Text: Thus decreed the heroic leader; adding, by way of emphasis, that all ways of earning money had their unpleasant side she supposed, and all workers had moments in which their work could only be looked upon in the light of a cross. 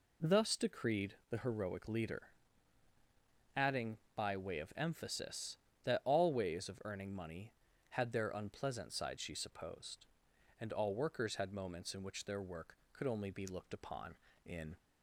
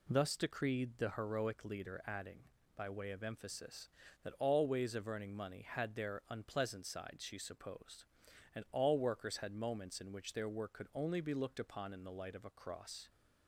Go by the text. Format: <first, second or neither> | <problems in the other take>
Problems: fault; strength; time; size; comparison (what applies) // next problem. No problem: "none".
second | pauses between "decreed" and "the"; slight; at 1.1 s; 0.16 s long // stops before "the light of a cross"; at 14.7 s